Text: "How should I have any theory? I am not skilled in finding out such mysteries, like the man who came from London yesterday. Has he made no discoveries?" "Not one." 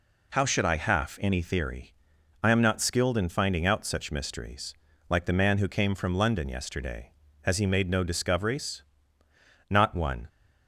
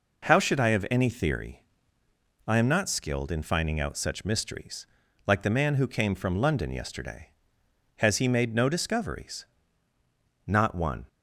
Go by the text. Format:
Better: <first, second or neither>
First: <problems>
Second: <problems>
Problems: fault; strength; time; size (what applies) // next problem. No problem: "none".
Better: second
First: says "half" for "have"; at 0.7 s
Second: none